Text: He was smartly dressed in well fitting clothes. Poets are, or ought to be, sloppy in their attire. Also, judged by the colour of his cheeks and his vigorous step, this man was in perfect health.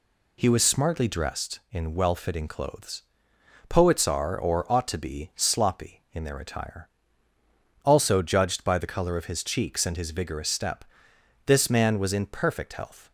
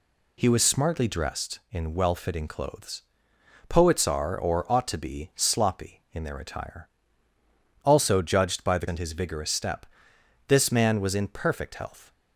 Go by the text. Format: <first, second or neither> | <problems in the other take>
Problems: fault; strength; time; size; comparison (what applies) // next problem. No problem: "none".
first | skips "colour of his cheeks"; at 8.8 s